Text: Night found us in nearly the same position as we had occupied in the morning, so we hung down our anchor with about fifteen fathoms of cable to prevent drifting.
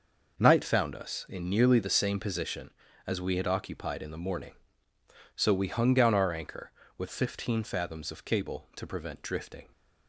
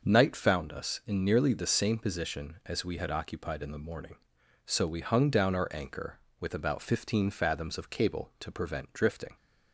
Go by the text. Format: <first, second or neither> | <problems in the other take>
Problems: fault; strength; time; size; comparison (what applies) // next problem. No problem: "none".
second | skips "about"; at 7.0 s